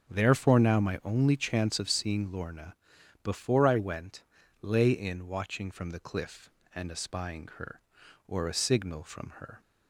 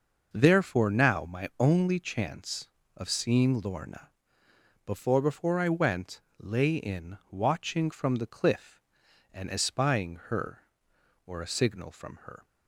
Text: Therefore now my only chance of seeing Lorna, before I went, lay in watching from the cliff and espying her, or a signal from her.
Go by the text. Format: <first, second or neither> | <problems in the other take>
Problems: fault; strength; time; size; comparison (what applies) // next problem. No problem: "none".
first | says "before" twice; at 5.1 s